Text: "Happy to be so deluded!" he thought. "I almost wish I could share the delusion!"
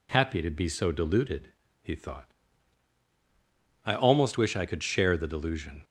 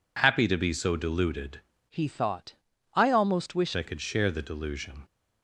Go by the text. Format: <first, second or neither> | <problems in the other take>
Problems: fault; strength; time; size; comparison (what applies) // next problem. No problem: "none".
first | changes voice from "he" to "wish"; from 1.9 to 3.7 s; 1.8 s long